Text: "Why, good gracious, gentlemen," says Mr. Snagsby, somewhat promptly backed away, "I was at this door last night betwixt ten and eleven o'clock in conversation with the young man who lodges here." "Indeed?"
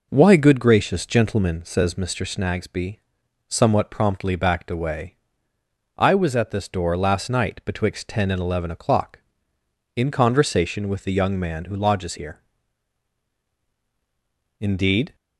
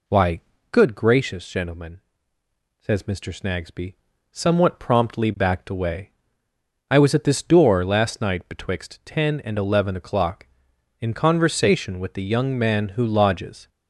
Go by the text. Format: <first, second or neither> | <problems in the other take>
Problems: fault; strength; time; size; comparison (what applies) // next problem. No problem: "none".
first | stops before "here Indeed"; at 13.6 s